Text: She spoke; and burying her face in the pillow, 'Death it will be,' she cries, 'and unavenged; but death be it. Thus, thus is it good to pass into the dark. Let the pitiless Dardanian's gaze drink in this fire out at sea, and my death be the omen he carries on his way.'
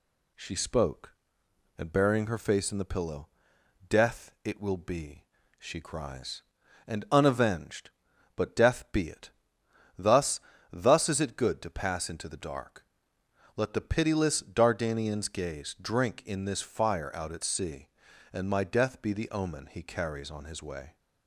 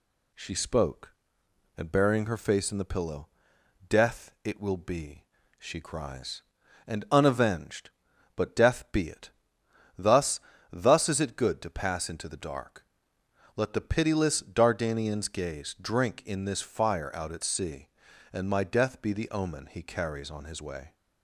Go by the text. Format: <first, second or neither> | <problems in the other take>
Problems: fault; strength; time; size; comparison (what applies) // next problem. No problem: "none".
neither | none